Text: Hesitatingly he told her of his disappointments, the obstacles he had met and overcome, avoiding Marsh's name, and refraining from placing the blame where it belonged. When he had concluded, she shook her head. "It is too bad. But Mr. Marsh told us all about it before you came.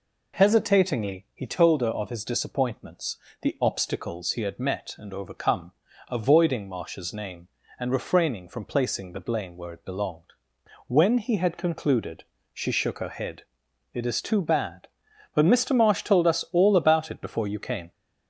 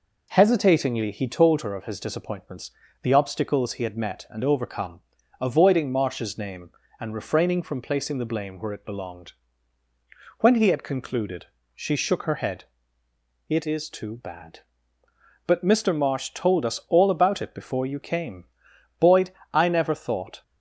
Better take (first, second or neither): first